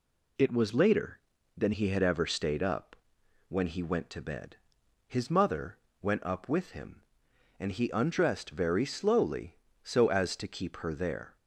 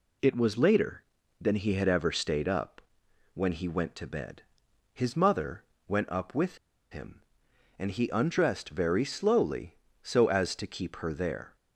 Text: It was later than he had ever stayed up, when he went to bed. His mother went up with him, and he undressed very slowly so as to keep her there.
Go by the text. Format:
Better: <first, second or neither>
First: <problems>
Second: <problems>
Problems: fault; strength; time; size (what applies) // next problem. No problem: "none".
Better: first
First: pauses between "mother" and "went"; slight; at 5.7 s; 0.24 s long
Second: pauses between "mother" and "went"; slight; at 5.6 s; 0.24 s long // pauses between "with" and "him"; slight; at 6.5 s; 0.33 s long